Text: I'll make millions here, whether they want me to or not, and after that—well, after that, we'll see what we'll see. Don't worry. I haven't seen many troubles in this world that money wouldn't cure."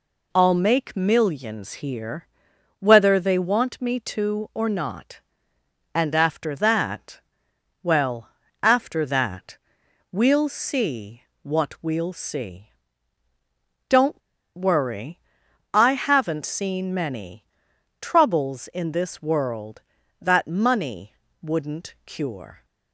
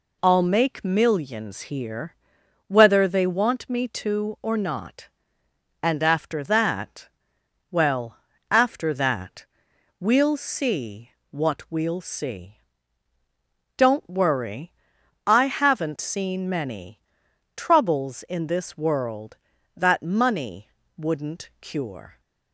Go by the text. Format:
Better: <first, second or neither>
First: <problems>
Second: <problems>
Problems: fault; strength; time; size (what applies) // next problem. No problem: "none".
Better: second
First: pauses between "see" and "what"; slight; at 11.2 s; 0.20 s long // pauses between "Don't" and "worry"; at 14.2 s; 0.37 s long // pauses between "many" and "troubles"; noticeable; at 17.4 s; 0.56 s long // pauses between "money" and "wouldn't"; slight; at 21.1 s; 0.30 s long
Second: pauses between "see" and "what"; slight; at 11.1 s; 0.20 s long // pauses between "many" and "troubles"; noticeable; at 17.0 s; 0.56 s long // pauses between "money" and "wouldn't"; slight; at 20.6 s; 0.30 s long